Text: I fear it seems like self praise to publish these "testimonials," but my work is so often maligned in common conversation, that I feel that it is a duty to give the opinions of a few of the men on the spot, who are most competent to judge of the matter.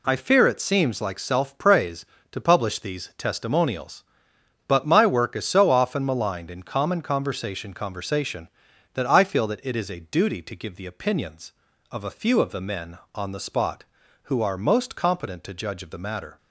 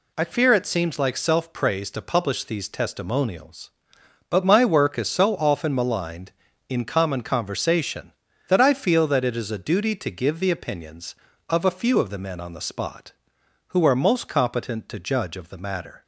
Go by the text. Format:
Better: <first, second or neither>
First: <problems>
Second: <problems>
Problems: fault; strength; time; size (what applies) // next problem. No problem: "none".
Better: second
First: says "conversation" twice; at 7.7 s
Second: none